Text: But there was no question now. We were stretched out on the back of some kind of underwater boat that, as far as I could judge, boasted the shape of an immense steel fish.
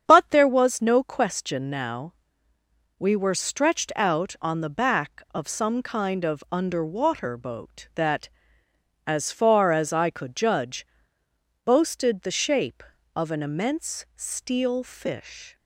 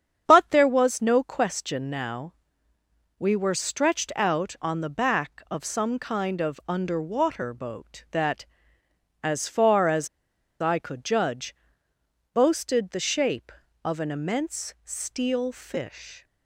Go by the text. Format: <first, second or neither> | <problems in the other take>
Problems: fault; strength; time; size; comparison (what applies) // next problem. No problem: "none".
first | starts louder than the rest; strong; until 1.2 s; 8 dB; strong in the first // pauses between "as" and "I"; noticeable; at 10.0 s; 0.53 s long